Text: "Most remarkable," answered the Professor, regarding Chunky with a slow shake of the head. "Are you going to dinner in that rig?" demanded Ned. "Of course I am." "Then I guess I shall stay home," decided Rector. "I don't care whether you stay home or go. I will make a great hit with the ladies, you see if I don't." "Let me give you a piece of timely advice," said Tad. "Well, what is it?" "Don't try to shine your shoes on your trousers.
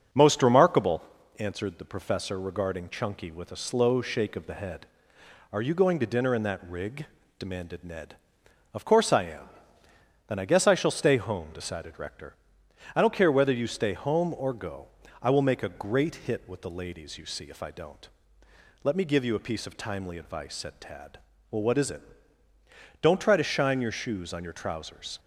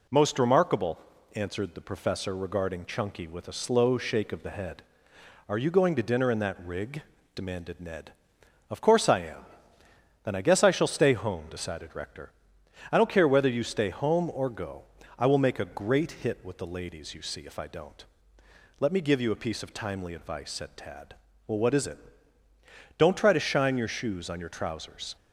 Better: second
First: starts louder than the rest; until 1.2 s; 6.5 dB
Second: none

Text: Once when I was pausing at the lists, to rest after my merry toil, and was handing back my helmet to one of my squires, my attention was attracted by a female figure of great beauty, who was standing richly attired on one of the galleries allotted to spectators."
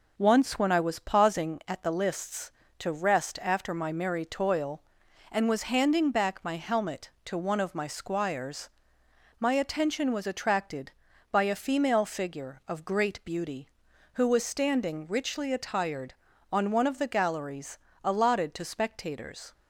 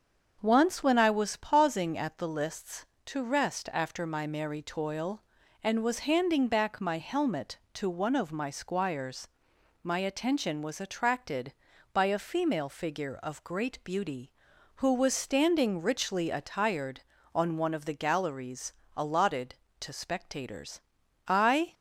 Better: first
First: pauses between "galleries" and "allotted"; slight; at 17.7 s; 0.24 s long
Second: starts louder than the rest; until 1.4 s; 7 dB // pauses between "galleries" and "allotted"; slight; at 18.7 s; 0.24 s long // goes on to say "I"; slight; from 21.2 s on; 0.46 s long

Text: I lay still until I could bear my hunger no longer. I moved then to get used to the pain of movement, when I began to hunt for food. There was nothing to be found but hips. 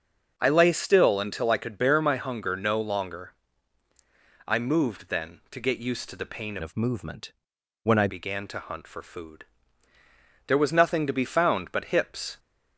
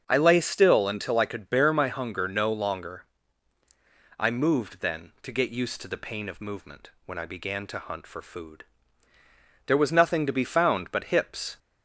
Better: second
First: starts louder than the rest; until 1.3 s; 6.5 dB // changes voice from "of" to "I"; from 6.6 to 8.0 s; 1.4 s long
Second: starts louder than the rest; strong; until 1.0 s; 7 dB

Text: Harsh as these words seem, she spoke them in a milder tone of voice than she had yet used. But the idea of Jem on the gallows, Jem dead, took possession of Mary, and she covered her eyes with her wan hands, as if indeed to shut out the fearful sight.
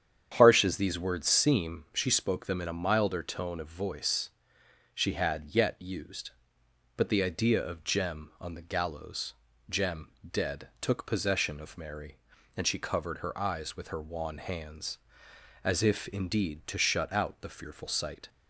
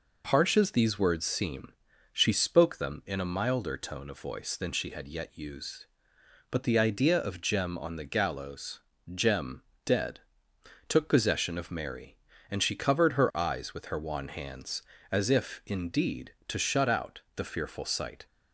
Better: second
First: starts louder than the rest; strong; until 1.3 s; 8.5 dB // skips "than"; at 4.6 s // pauses between "Jem" and "dead"; slight; at 10.0 s; 0.22 s long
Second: pauses between "Jem" and "dead"; slight; at 9.6 s; 0.24 s long

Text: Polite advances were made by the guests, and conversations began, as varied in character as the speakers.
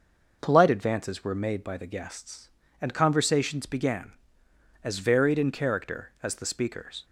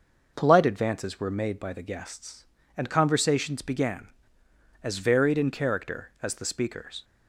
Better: neither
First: none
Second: none

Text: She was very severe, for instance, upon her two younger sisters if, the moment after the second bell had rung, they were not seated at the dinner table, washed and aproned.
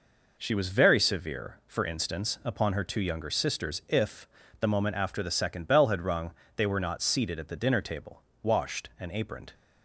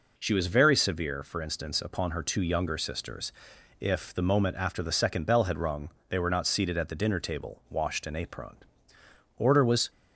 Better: first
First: none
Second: pauses between "sisters" and "if"; noticeable; at 3.3 s; 0.48 s long // goes on to say "Order was"; from 9.3 s on; 0.52 s long

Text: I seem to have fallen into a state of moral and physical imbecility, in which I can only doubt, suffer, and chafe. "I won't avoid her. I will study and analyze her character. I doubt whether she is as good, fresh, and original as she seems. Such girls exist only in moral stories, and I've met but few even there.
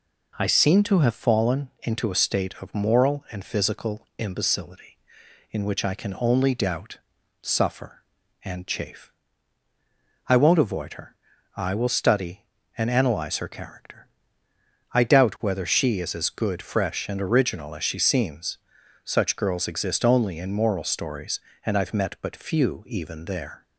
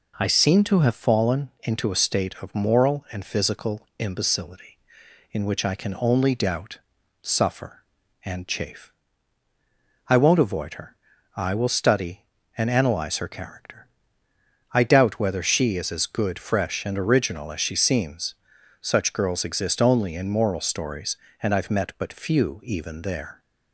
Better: neither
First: none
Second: none

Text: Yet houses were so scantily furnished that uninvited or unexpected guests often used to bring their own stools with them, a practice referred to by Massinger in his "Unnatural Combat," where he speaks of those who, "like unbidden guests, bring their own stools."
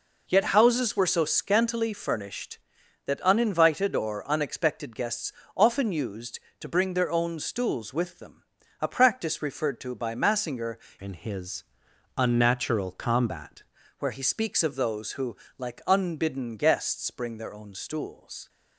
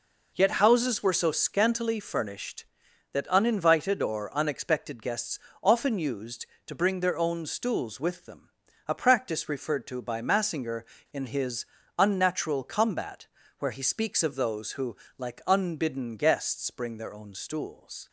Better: second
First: pauses between "guests" and "often"; slight; at 5.3 s; 0.24 s long // changes voice from "in" to "Combat"; from 11.0 to 13.6 s; 2.6 s long // pauses between "his" and "Unnatural"; noticeable; at 11.6 s; 0.52 s long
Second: pauses between "guests" and "often"; slight; at 5.3 s; 0.24 s long // pauses between "his" and "Unnatural"; slight; at 11.6 s; 0.34 s long

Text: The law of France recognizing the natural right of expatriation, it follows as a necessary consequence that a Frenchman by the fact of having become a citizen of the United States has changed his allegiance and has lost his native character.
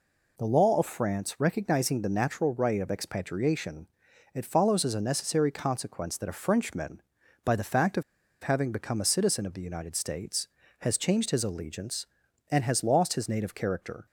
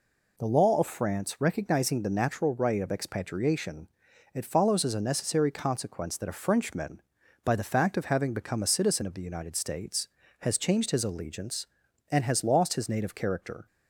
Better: second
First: pauses between "of" and "having"; at 8.0 s; 0.40 s long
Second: none

